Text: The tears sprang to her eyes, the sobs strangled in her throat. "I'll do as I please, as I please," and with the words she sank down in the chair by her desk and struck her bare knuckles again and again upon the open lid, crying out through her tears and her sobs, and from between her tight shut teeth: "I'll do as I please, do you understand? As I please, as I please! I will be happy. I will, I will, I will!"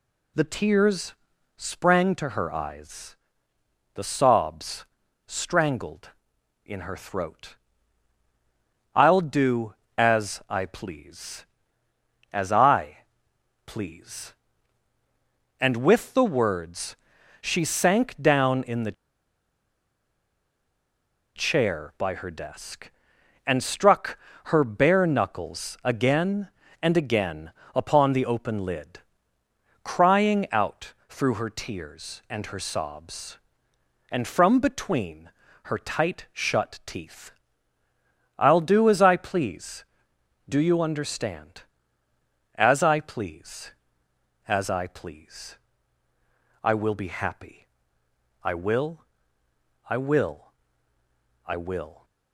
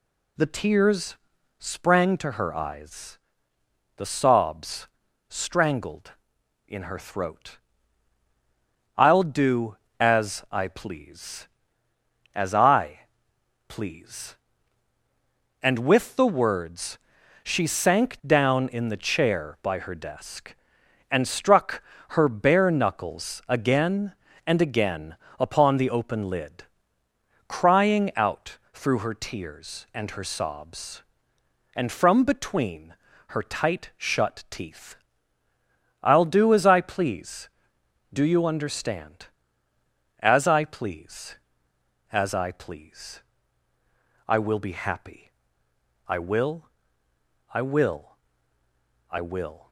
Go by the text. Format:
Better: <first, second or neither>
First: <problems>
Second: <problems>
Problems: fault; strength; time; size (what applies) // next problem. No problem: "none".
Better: second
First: pauses between "tears" and "sprang"; at 1.1 s; 0.44 s long // pauses between "sobs" and "strangled"; at 4.8 s; 0.44 s long // pauses between "I" and "please"; noticeable; at 13.0 s; 0.60 s long // pauses between "words" and "she"; at 16.9 s; 0.44 s long // pauses between "the" and "chair"; strong; at 18.9 s; 2.4 s long // pauses between "struck" and "her"; slight; at 24.1 s; 0.28 s long // pauses between "again" and "upon"; slight; at 27.5 s; 0.20 s long // pauses between "out" and "through"; slight; at 30.9 s; 0.16 s long // pauses between "between" and "her"; slight; at 35.3 s; 0.34 s long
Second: pauses between "tears" and "sprang"; at 1.1 s; 0.44 s long // pauses between "sobs" and "strangled"; at 4.8 s; 0.44 s long // pauses between "I" and "please"; noticeable; at 13.0 s; 0.60 s long // pauses between "words" and "she"; at 16.9 s; 0.44 s long // pauses between "struck" and "her"; slight; at 21.8 s; 0.28 s long // pauses between "again" and "upon"; slight; at 25.1 s; 0.20 s long // pauses between "out" and "through"; slight; at 28.5 s; 0.16 s long // pauses between "between" and "her"; slight; at 32.9 s; 0.34 s long